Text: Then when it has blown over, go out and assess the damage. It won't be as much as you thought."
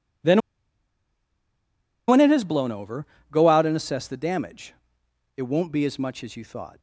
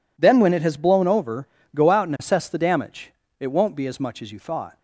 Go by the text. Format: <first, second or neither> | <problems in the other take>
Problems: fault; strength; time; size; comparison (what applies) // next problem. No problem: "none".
second | pauses between "Then" and "when"; strong; at 0.4 s; 1.6 s long